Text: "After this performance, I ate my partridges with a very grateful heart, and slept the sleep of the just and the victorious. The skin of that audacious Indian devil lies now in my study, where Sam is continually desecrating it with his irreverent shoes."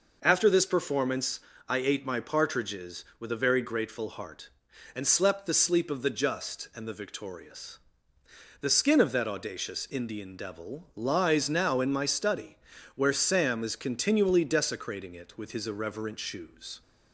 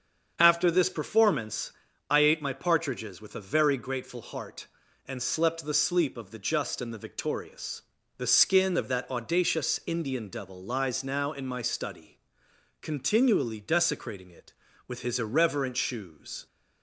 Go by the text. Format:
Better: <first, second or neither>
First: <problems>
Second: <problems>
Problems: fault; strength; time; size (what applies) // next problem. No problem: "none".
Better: first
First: none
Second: starts louder than the rest; until 1.4 s; 7 dB // skips "where Sam is"; at 12.4 s